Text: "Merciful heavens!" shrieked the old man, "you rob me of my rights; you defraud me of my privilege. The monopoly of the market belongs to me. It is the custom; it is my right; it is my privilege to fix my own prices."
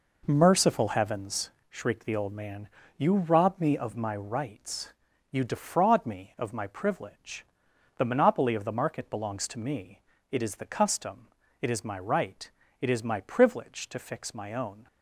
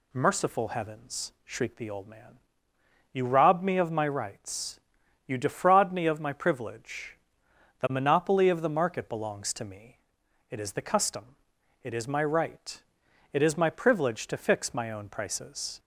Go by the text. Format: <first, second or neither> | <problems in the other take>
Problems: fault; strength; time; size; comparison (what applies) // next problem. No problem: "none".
second | stops before "prices"; at 14.8 s